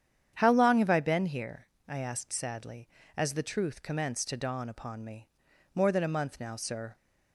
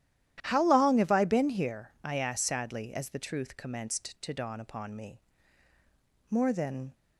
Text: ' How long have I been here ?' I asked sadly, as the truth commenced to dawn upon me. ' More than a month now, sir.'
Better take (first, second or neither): first